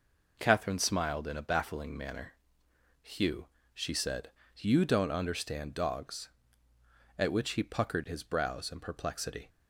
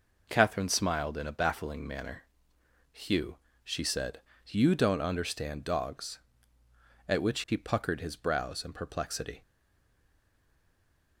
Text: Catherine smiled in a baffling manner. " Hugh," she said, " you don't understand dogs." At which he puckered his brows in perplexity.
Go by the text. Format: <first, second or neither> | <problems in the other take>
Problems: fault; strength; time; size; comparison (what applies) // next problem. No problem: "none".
first | stays silent after the last word; noticeable; from 9.4 s on; 1.7 s long